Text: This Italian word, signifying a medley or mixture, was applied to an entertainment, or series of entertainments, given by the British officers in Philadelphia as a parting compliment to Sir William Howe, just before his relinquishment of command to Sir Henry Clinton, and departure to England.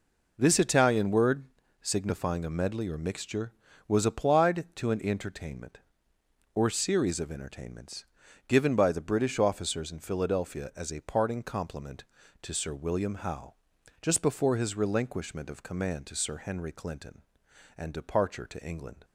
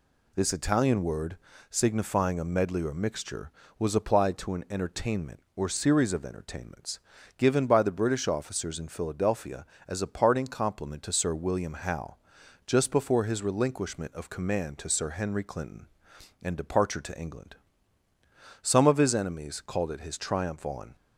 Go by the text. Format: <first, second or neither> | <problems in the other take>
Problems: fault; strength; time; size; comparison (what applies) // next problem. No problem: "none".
first | goes on to say "Some of his enemies called it his triumph on"; strong; from 18.6 s on; 2.3 s long